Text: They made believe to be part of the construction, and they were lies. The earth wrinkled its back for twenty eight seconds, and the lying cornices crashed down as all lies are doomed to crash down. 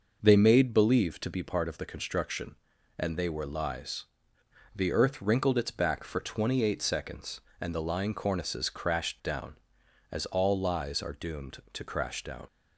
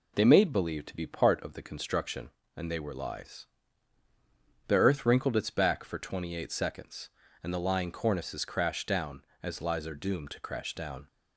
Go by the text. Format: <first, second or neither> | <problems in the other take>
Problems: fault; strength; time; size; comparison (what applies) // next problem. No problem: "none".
first | skips "all"; at 9.6 s